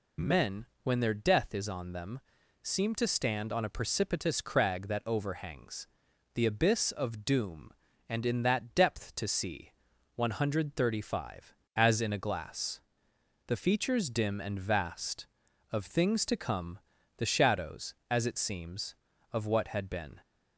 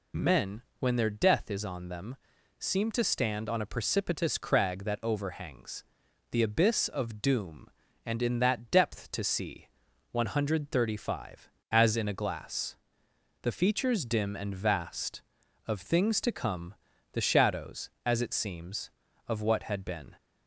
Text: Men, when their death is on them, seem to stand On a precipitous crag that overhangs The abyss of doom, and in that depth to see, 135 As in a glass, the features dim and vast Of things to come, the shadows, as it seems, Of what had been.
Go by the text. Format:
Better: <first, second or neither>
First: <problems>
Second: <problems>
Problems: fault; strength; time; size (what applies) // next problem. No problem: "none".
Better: neither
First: pauses between "overhangs" and "The"; noticeable; at 5.8 s; 0.48 s long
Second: pauses between "overhangs" and "The"; noticeable; at 5.8 s; 0.48 s long